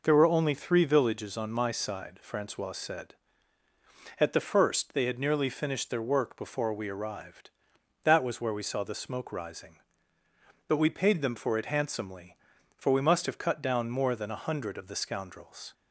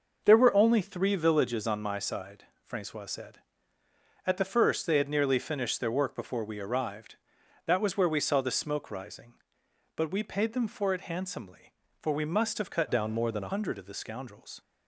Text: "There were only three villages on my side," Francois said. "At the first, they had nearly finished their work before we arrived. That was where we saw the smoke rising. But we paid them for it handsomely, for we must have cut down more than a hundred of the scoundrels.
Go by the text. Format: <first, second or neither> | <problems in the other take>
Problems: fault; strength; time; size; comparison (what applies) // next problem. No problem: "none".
first | changes voice from "down" to "a"; from 12.8 to 13.5 s; 0.7 s long